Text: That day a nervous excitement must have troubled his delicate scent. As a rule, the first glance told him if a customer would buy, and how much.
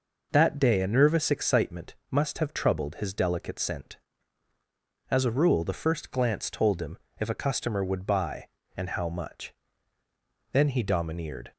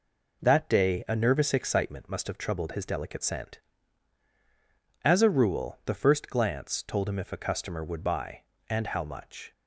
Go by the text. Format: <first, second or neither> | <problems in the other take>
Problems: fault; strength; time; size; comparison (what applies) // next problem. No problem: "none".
second | pauses between "excitement" and "must"; slight; at 1.9 s; 0.16 s long // pauses between "him" and "if"; slight; at 6.9 s; 0.20 s long // goes on to say "Then he domineered"; noticeable; from 10.5 s on; 1.0 s long